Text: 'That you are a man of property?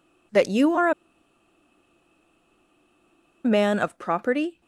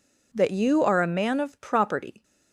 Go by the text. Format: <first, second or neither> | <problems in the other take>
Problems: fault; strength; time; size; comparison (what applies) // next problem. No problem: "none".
second | pauses between "a" and "man"; strong; at 0.9 s; 2.5 s long